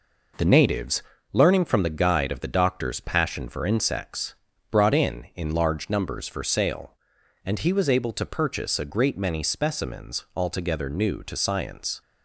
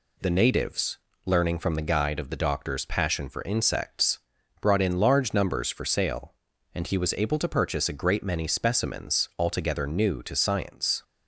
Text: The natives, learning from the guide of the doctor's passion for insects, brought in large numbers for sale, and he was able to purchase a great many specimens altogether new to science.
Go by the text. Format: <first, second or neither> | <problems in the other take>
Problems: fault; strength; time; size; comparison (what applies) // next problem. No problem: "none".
second | says "in" twice; at 5.3 s